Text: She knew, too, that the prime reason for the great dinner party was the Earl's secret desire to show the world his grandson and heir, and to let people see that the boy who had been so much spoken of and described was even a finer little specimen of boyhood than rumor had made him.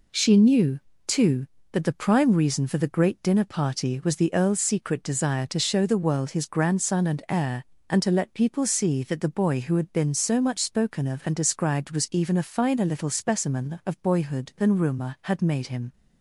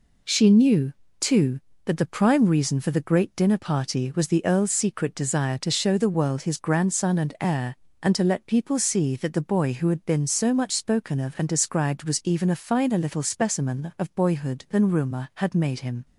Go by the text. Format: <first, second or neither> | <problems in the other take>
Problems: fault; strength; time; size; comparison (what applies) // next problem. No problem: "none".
neither | none